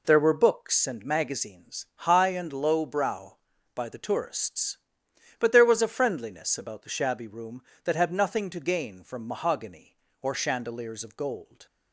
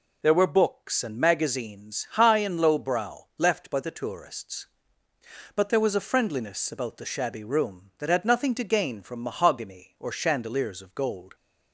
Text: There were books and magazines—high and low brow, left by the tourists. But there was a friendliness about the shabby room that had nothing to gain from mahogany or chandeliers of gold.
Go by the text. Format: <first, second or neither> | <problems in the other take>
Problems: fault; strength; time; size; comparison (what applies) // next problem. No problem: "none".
second | skips "left"; at 3.5 s